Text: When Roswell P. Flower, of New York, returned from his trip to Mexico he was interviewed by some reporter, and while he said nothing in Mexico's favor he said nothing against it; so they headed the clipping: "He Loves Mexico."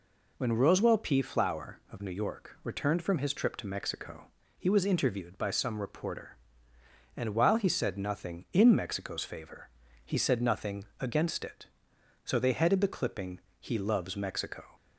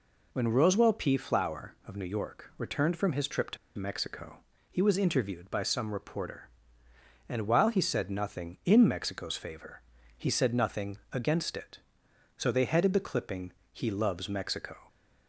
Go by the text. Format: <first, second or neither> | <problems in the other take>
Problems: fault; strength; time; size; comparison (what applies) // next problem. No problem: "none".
first | pauses between "to" and "Mexico"; slight; at 3.5 s; 0.21 s long // pauses between "Mexico" and "he"; slight; at 4.3 s; 0.32 s long; slight in the first // pauses between "favor" and "he"; slight; at 9.8 s; 0.34 s long; slight in the first // pauses between "nothing" and "against"; slight; at 10.9 s; 0.16 s long; slight in the first